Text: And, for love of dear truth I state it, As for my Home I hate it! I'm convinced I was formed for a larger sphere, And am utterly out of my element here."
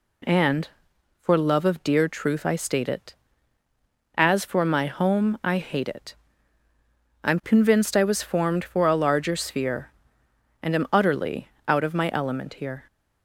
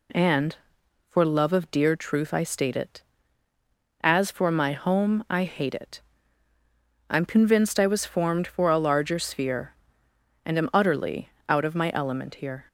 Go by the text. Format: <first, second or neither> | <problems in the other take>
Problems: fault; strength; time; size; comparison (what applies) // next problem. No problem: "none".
neither | pauses between "utterly" and "out"; slight; the same in both